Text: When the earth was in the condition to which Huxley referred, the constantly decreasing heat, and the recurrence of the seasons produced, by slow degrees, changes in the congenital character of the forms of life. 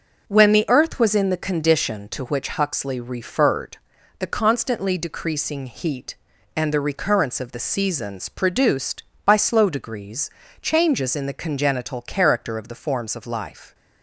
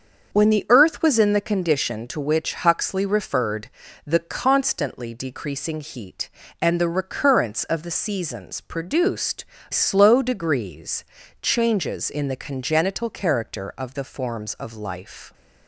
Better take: first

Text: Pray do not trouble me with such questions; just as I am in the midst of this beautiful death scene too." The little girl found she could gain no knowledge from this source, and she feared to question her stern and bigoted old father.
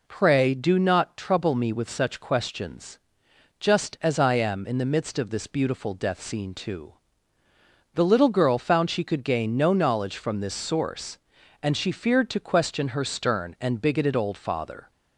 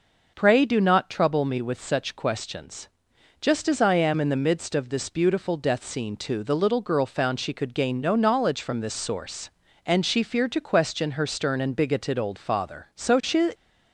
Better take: first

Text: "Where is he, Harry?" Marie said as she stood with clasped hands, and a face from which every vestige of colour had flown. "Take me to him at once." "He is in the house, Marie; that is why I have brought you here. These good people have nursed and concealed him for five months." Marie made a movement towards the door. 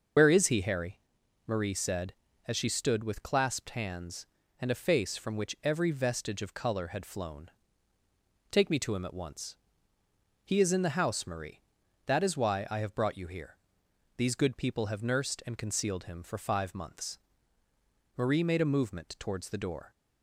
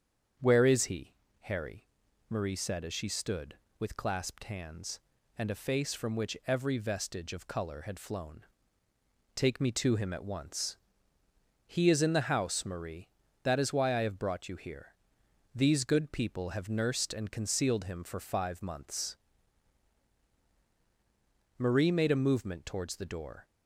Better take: second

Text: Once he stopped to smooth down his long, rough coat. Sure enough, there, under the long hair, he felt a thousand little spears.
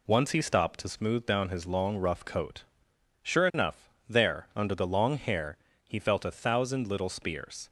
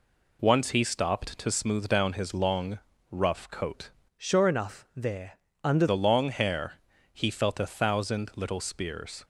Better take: first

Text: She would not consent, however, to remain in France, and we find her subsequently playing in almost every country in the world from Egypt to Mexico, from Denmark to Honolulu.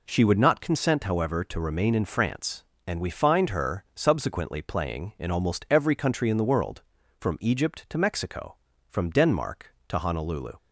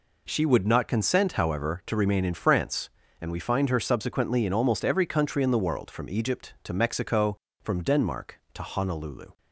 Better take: first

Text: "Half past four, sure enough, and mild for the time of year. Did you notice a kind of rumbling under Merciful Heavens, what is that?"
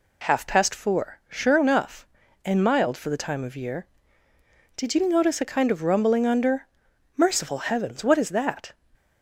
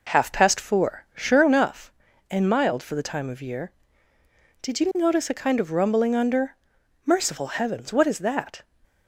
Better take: first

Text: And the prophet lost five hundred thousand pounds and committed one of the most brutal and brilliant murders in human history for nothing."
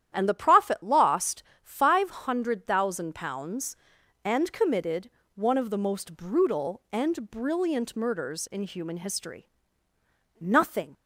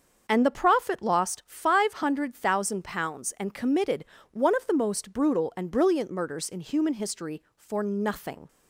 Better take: second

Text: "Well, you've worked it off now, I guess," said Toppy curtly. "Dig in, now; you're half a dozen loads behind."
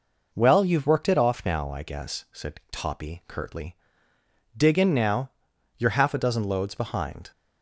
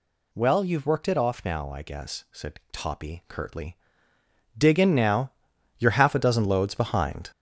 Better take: first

